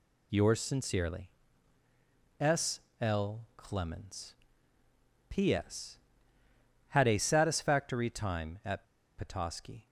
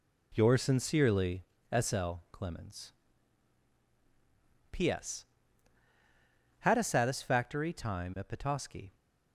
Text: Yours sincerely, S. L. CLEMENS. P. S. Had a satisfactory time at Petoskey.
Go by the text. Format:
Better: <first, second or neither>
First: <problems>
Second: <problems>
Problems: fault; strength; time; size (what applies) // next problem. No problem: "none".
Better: second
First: pauses between "S" and "L"; slight; at 2.7 s; 0.22 s long // pauses between "L" and "CLEMENS"; slight; at 3.3 s; 0.16 s long // pauses between "at" and "Petoskey"; slight; at 8.8 s; 0.34 s long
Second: none